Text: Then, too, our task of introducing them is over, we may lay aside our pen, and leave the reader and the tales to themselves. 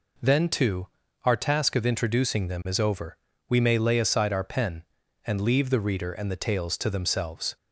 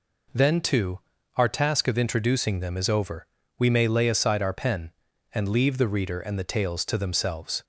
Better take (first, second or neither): neither